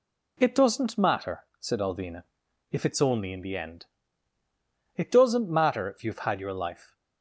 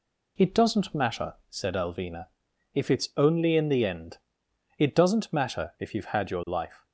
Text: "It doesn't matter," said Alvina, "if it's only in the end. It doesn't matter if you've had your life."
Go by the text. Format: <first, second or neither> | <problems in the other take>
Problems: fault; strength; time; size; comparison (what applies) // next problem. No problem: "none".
neither | none